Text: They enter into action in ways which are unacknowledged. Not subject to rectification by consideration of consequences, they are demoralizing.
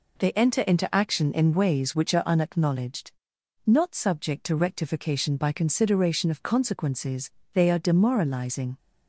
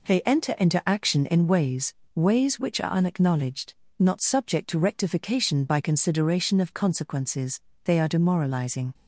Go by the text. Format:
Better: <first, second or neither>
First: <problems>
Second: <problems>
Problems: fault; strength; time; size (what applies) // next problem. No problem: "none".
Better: first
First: none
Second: says "ways" twice; at 2.1 s